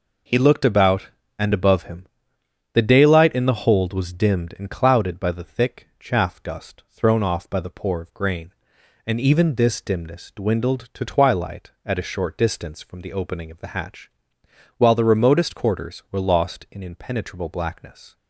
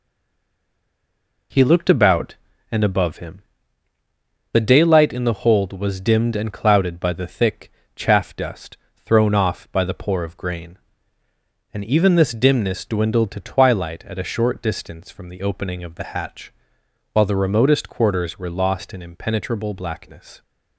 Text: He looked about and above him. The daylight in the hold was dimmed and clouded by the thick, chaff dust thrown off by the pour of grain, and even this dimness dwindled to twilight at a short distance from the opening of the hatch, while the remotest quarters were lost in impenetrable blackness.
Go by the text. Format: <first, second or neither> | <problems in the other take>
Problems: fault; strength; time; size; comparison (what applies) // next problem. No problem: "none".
first | stays silent before the first word; noticeable; until 1.5 s; 1.5 s long // pauses between "dust" and "thrown"; slight; at 8.7 s; 0.28 s long